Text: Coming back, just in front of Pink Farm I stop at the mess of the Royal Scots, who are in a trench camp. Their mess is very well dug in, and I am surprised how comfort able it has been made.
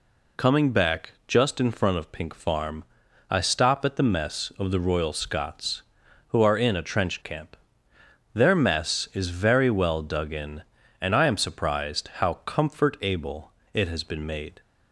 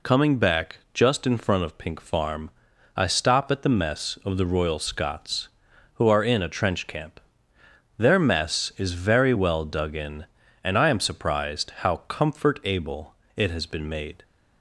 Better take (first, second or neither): neither